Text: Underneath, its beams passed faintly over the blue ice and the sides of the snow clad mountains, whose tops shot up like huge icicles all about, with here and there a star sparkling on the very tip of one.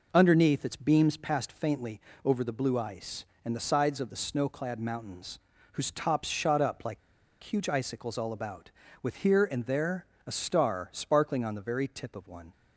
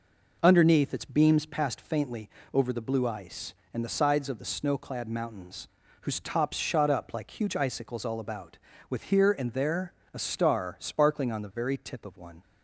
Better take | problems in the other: second | pauses between "faintly" and "over"; slight; at 1.9 s; 0.24 s long; slight in the second // pauses between "like" and "huge"; at 6.9 s; 0.43 s long // pauses between "there" and "a"; slight; at 10.0 s; 0.20 s long; slight in the second

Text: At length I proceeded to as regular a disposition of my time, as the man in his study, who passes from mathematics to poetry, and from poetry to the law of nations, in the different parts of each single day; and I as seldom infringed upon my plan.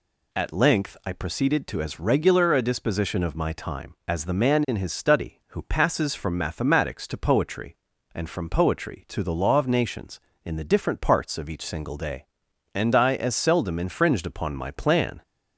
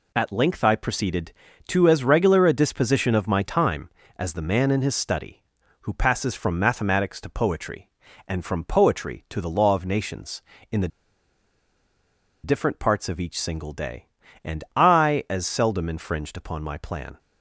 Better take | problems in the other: first | pauses between "the" and "different"; strong; at 10.8 s; 1.5 s long

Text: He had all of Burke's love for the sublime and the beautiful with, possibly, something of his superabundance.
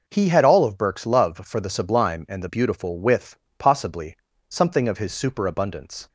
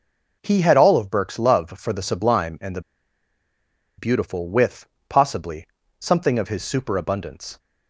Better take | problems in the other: first | pauses between "the" and "beautiful"; at 2.8 s; 1.1 s long

